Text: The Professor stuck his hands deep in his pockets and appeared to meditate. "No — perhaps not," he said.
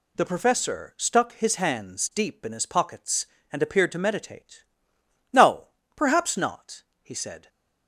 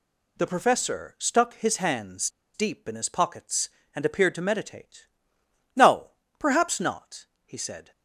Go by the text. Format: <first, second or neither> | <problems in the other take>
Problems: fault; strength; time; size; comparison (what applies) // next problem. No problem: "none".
first | pauses between "hands" and "deep"; slight; at 2.2 s; 0.26 s long